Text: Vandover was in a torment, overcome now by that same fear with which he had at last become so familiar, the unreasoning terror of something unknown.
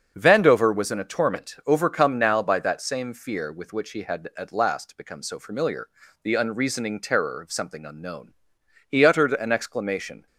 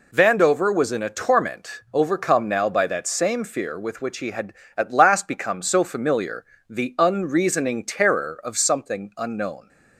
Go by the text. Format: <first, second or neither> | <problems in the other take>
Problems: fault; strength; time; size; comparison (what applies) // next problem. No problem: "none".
second | starts louder than the rest; until 1.1 s; 7 dB // goes on to say "He uttered an exclamation"; from 8.8 s on; 1.3 s long